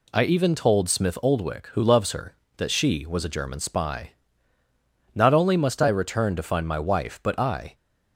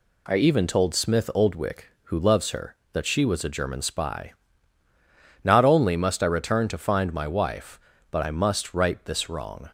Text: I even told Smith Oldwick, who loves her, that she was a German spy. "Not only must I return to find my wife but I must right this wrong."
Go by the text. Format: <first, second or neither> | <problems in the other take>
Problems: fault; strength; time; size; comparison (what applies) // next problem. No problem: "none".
second | stops before "must right this wrong"; at 7.7 s